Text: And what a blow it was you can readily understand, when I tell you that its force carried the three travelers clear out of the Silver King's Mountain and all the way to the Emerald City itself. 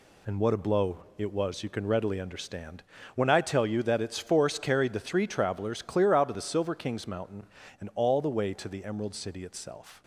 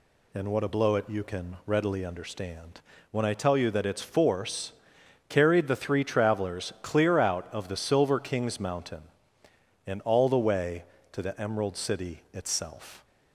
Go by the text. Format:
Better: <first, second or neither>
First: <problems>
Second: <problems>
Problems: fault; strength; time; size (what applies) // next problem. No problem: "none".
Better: first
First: none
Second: skips "was"; at 1.0 s // pauses between "force" and "carried"; noticeable; at 4.7 s; 0.58 s long